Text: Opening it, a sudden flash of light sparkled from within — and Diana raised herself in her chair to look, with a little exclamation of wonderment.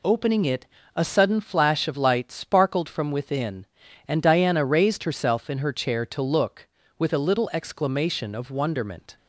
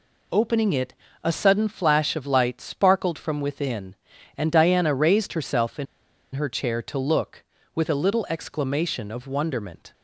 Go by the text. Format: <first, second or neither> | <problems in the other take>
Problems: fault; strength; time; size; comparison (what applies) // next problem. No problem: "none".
first | pauses between "in" and "her"; noticeable; at 5.8 s; 0.49 s long